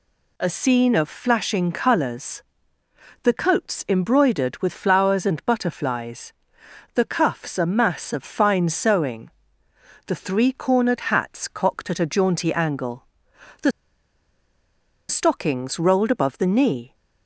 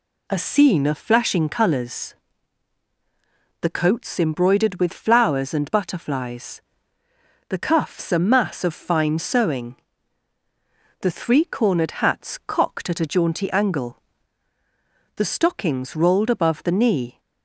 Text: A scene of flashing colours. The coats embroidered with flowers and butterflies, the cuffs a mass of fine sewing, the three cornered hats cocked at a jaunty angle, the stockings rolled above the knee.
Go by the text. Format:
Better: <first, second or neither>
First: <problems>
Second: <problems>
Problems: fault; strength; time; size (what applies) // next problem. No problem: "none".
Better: second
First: pauses between "the" and "stockings"; strong; at 13.7 s; 1.3 s long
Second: none